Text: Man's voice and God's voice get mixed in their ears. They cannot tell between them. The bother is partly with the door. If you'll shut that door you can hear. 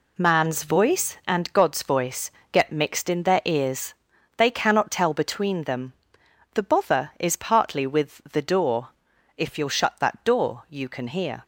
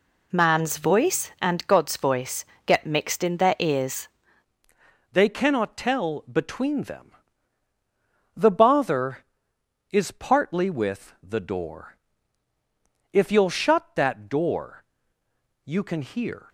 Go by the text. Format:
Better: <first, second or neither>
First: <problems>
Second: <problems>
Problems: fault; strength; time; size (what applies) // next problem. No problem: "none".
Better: first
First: pauses between "voice" and "get"; slight; at 2.3 s; 0.20 s long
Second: pauses between "voice" and "get"; slight; at 2.4 s; 0.20 s long // changes voice at "They"; from 5.1 s on; 11.3 s long // pauses between "door" and "you"; noticeable; at 14.8 s; 0.82 s long